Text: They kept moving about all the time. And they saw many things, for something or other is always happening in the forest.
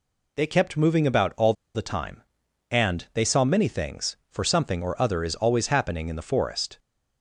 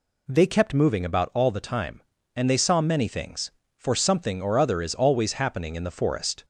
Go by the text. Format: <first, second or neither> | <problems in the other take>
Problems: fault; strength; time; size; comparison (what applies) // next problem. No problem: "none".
second | pauses between "all" and "the"; slight; at 1.5 s; 0.22 s long